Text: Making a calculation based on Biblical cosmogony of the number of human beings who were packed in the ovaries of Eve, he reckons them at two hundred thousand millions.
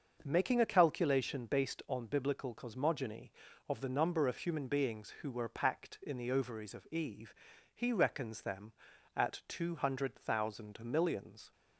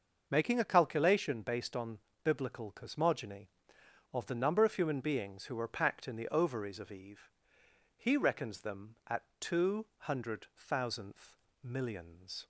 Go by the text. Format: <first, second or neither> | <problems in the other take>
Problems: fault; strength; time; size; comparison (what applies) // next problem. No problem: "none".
first | starts louder than the rest; until 1.3 s; 6.5 dB; also in the first // pauses between "on" and "Biblical"; slight; at 1.9 s; 0.24 s long // pauses between "at" and "two"; slight; at 9.2 s; 0.16 s long // says "thousandth" for "thousand"; at 10.5 s